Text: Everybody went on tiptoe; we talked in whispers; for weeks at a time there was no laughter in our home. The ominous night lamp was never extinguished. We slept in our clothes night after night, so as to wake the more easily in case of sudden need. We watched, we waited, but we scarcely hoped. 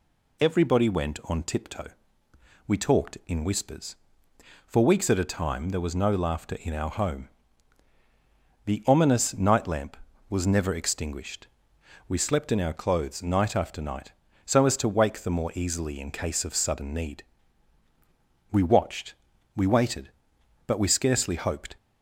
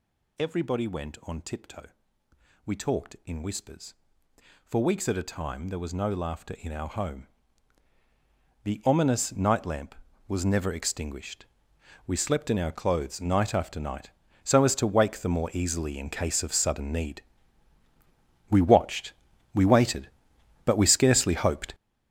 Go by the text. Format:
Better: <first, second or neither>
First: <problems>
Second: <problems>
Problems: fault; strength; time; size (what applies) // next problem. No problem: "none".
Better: first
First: none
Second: gets louder; strong; throughout; 11.5 dB